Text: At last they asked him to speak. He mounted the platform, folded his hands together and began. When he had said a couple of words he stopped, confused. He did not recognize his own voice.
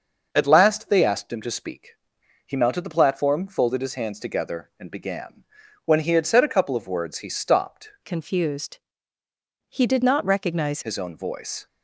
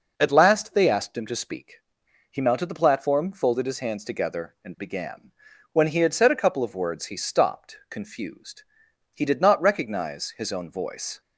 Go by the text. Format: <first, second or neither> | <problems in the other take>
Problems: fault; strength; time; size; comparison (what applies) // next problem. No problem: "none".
second | starts louder than the rest; noticeable; until 1.3 s; 6 dB // changes voice from "confused" to "recognize"; from 8.0 to 10.8 s; 2.8 s long